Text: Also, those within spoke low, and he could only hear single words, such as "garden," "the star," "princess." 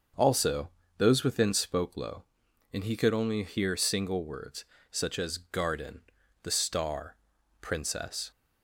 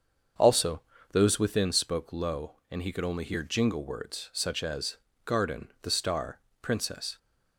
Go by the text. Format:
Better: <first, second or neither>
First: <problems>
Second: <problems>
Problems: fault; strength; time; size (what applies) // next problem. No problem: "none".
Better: first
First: starts louder than the rest; until 1.4 s; 6.5 dB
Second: starts louder than the rest; until 1.6 s; 7 dB // says "jingle" for "single"; at 3.4 s // pauses between "as" and "garden"; slight; at 4.9 s; 0.26 s long